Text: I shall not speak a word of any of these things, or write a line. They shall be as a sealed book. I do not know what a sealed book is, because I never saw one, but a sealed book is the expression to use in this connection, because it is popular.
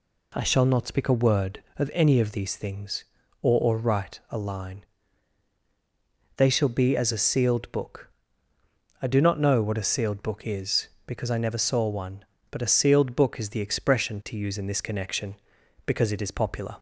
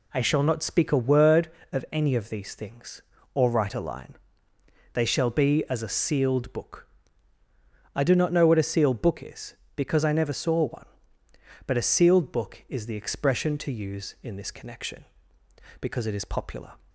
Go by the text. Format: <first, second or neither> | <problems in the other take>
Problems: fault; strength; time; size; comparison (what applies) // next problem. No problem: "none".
second | says "or" twice; at 3.6 s